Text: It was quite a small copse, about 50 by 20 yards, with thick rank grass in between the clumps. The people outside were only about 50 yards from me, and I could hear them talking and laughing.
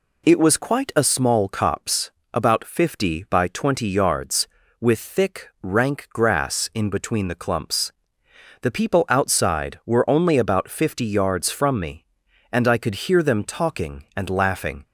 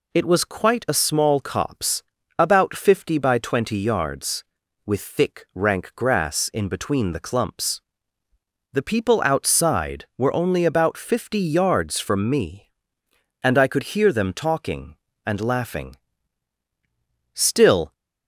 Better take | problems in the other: first | goes on to say "Still"; from 17.3 s on; 0.60 s long

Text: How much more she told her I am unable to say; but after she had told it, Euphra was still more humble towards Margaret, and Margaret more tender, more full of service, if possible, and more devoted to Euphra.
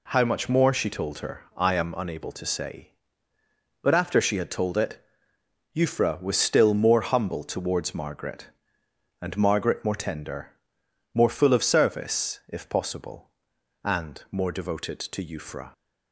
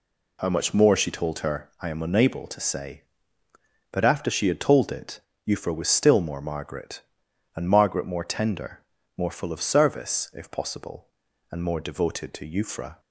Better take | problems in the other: first | skips "humble towards"; at 6.3 s

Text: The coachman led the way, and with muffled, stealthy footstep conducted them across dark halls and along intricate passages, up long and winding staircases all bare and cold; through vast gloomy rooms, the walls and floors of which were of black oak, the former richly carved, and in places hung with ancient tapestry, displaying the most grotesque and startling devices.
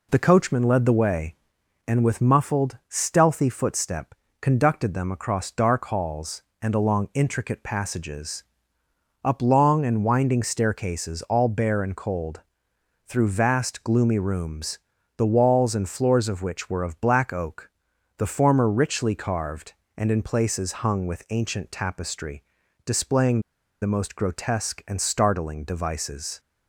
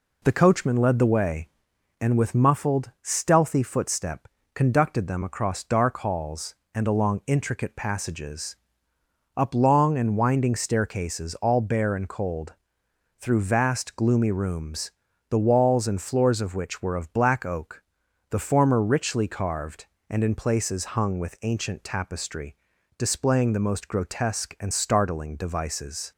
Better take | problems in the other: second | pauses between "footstep" and "conducted"; slight; at 4.1 s; 0.26 s long; slight in the second // pauses between "displaying" and "the"; at 23.3 s; 0.42 s long

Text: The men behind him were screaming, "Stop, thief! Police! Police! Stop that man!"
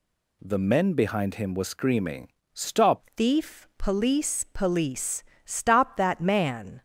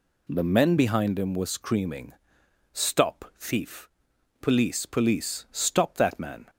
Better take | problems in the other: second | changes voice at "thief"; from 3.1 s on; 3.7 s long

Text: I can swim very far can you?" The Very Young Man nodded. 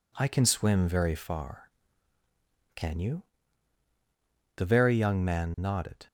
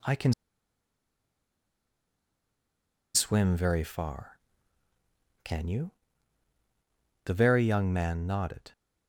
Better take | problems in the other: first | pauses between "can" and "swim"; strong; at 0.3 s; 2.8 s long

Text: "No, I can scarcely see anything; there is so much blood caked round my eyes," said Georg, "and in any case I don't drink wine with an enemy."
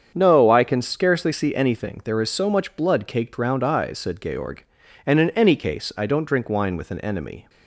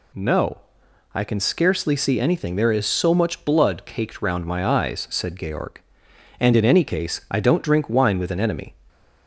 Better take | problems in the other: second | starts louder than the rest; strong; until 1.1 s; 7.5 dB // skips "my"; at 3.6 s

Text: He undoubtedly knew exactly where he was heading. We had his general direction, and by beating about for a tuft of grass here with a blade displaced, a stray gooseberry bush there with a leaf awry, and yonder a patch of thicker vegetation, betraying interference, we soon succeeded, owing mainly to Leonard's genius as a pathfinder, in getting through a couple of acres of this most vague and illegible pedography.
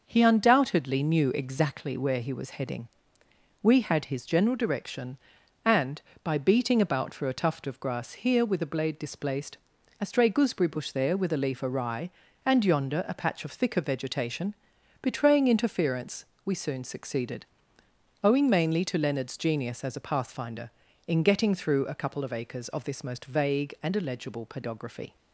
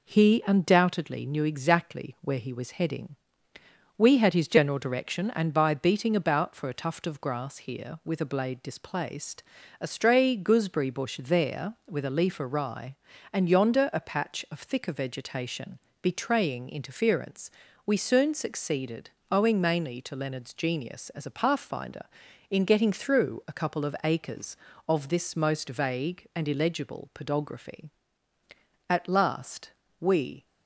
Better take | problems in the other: first | goes on to say "At last we"; from 28.8 s on; 1.5 s long

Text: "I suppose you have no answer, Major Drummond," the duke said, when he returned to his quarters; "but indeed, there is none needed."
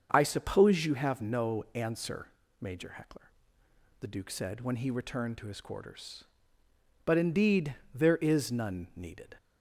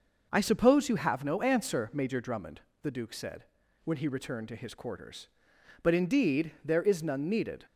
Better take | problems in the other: second | starts louder than the rest; until 1.1 s; 7 dB // says "Heckler" for "Drummond"; at 2.9 s

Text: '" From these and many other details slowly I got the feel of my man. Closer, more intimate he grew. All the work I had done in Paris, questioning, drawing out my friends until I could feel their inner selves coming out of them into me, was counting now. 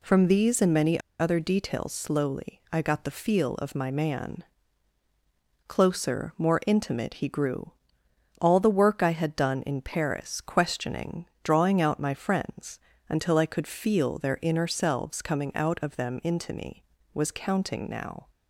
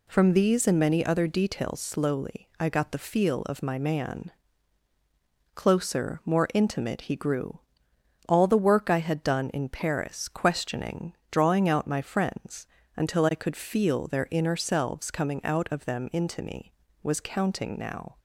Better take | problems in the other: second | pauses between "many" and "other"; slight; at 0.9 s; 0.20 s long // pauses between "friends" and "until"; slight; at 12.7 s; 0.30 s long; slight in the second

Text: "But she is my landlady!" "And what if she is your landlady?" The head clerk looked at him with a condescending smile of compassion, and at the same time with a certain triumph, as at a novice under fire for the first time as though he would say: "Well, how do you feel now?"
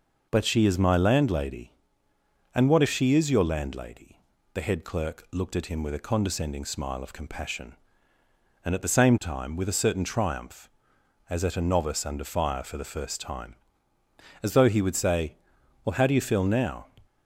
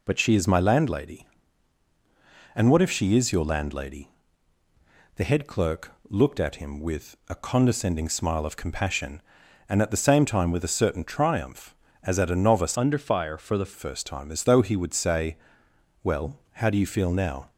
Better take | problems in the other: first | pauses between "clerk" and "looked"; slight; at 5.9 s; 0.16 s long // changes voice from "under" to "the"; from 12.7 to 13.7 s; 1.0 s long

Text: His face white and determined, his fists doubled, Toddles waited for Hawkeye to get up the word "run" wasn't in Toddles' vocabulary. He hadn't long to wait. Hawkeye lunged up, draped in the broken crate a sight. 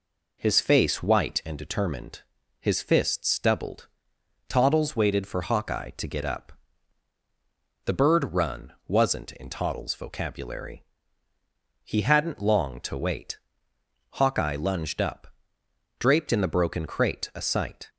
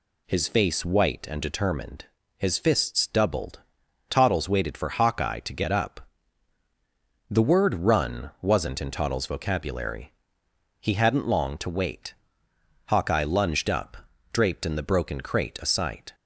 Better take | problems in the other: second | pauses between "up" and "the"; strong; at 6.5 s; 1.3 s long; strong in the second // says "bird" for "word"; at 7.9 s // pauses between "run" and "wasn't"; slight; at 8.7 s; 0.16 s long

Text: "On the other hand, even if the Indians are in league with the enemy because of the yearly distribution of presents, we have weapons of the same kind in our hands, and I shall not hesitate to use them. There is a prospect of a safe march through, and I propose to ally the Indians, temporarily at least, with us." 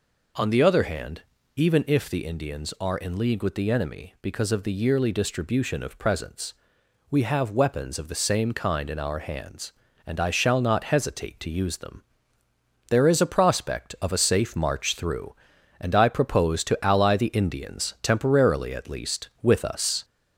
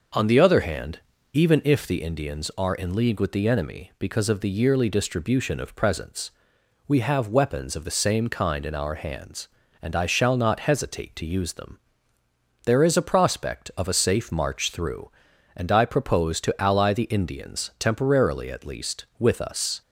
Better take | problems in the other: second | gets louder; slight; throughout; 2 dB

